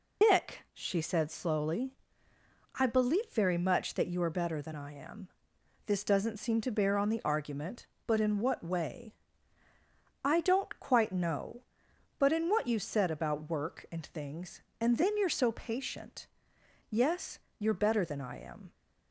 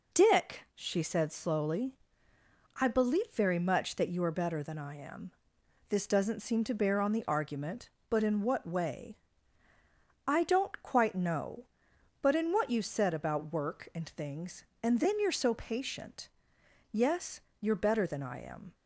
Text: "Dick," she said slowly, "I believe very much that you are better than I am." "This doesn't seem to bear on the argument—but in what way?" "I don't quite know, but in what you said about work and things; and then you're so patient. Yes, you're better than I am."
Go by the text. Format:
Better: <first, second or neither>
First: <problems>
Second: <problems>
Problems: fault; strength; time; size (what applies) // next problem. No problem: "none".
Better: second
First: loses the start of "Dick"; at 0.2 s; 90 ms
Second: none